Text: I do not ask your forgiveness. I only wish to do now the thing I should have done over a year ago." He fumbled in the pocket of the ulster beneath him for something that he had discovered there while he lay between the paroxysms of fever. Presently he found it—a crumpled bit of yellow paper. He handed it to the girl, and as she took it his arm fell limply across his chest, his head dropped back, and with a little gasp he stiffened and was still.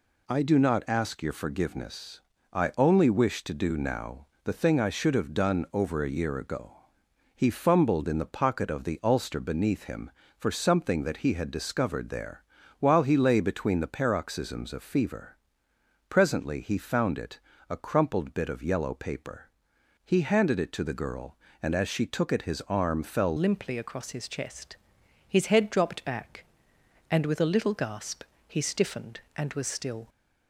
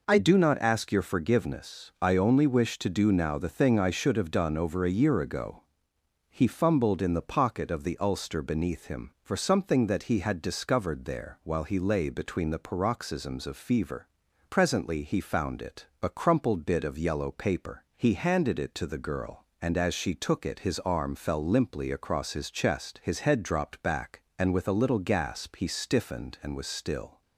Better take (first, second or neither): second